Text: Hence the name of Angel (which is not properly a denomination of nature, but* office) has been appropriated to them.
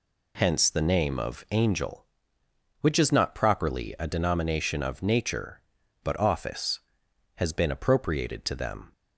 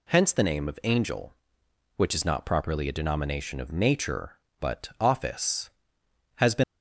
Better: first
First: none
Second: stops before "appropriated to them"; at 6.6 s

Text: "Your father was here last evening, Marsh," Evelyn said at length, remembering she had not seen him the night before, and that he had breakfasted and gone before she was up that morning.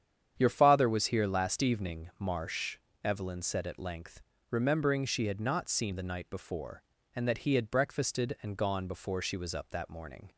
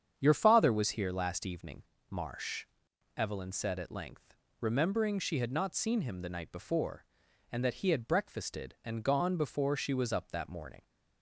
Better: second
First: starts louder than the rest; strong; until 1.3 s; 8.5 dB // skips "him"; at 5.9 s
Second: starts louder than the rest; strong; until 1.1 s; 8 dB

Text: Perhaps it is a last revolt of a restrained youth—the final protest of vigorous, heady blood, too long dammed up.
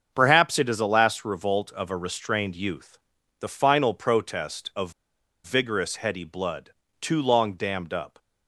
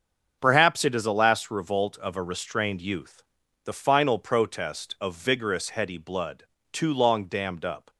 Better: second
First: starts louder than the rest; until 1.1 s; 6.5 dB // pauses between "of" and "vigorous"; noticeable; at 4.9 s; 0.53 s long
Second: starts louder than the rest; until 1.4 s; 6.5 dB

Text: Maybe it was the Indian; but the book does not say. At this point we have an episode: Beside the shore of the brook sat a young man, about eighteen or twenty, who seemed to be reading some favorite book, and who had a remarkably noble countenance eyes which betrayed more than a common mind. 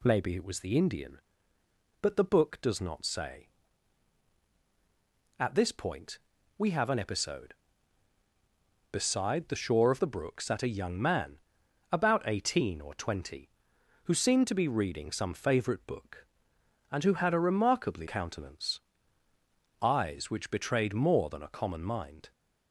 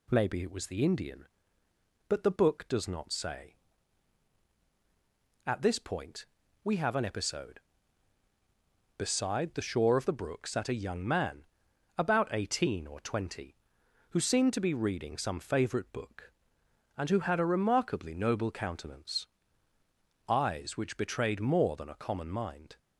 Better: second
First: pauses between "point" and "we"; at 6.1 s; 0.40 s long // skips "noble"; at 18.0 s // pauses between "countenance" and "eyes"; at 18.7 s; 1.0 s long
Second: pauses between "point" and "we"; at 6.2 s; 0.38 s long // pauses between "countenance" and "eyes"; at 19.2 s; 1.0 s long

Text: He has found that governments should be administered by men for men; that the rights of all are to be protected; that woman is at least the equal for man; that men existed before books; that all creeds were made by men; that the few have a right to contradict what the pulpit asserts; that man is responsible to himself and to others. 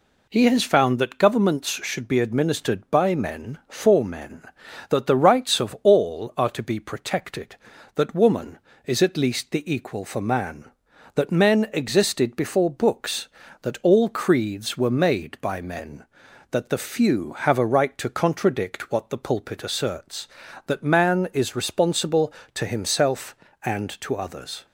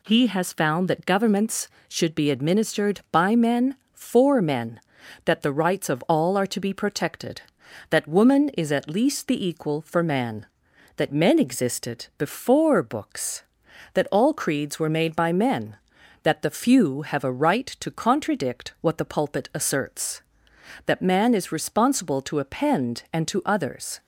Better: first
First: none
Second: says "append" for "himself"; at 22.3 s

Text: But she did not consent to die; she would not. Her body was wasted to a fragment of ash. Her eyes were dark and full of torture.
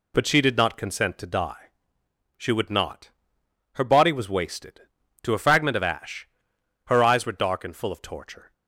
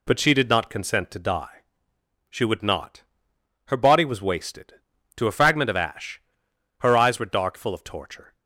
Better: first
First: none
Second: skips "and"; at 7.5 s

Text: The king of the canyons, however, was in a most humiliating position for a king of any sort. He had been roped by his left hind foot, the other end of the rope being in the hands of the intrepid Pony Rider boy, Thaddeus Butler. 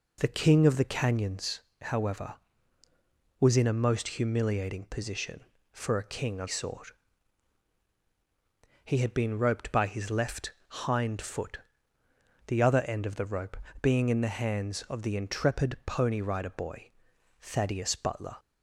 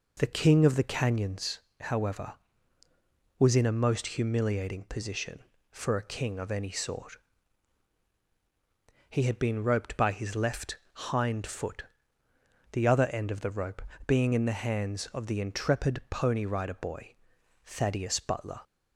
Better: second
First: skips "any"; at 6.4 s // pauses between "left" and "hind"; slight; at 10.5 s; 0.18 s long // pauses between "rope" and "being"; slight; at 13.5 s; 0.28 s long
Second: pauses between "left" and "hind"; slight; at 10.7 s; 0.18 s long // pauses between "rope" and "being"; slight; at 13.8 s; 0.28 s long

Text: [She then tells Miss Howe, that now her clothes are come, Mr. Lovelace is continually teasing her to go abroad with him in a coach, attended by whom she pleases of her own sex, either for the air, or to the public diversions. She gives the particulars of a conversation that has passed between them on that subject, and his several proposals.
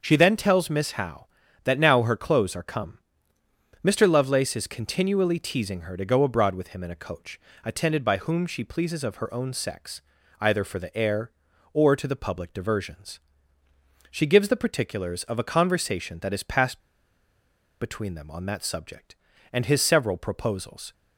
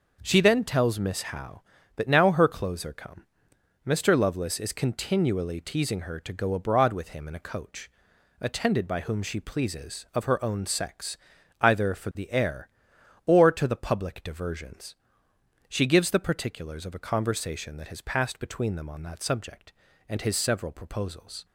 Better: second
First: starts louder than the rest; until 1.0 s; 6.5 dB // pauses between "passed" and "between"; at 16.7 s; 1.0 s long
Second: none

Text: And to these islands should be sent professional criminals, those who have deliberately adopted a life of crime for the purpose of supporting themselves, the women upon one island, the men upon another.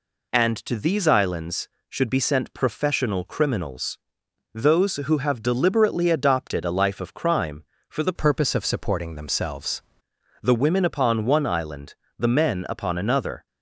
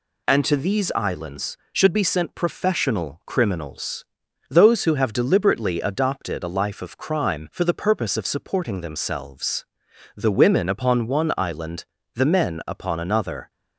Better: second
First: changes voice from "purpose" to "themselves"; from 8.1 to 9.8 s; 1.7 s long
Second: none

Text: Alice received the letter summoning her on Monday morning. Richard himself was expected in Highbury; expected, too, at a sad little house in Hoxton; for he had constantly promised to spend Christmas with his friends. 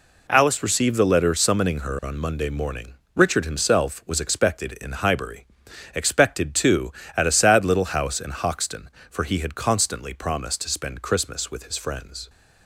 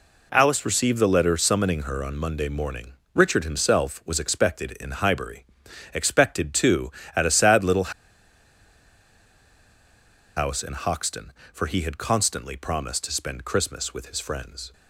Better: first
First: none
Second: pauses between "little" and "house"; strong; at 7.9 s; 2.4 s long

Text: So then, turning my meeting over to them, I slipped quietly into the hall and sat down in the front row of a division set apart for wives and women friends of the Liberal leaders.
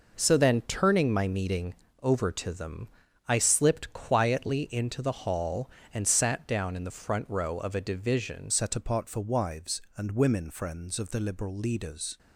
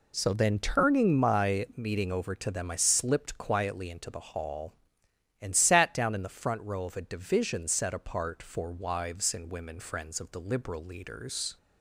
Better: second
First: pauses between "meeting" and "over"; slight; at 1.7 s; 0.26 s long // changes voice at "set"; from 8.5 s on; 3.6 s long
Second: none

